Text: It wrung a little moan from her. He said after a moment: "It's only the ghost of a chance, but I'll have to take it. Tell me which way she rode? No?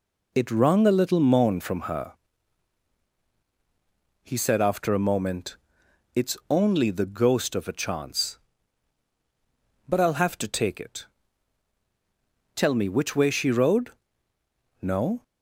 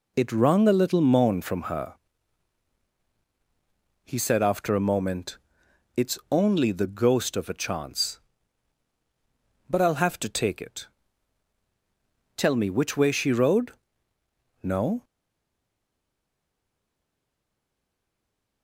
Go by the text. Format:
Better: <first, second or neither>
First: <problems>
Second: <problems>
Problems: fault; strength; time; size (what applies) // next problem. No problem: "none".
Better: first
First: none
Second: stays silent after the last word; strong; from 15.0 s on; 3.6 s long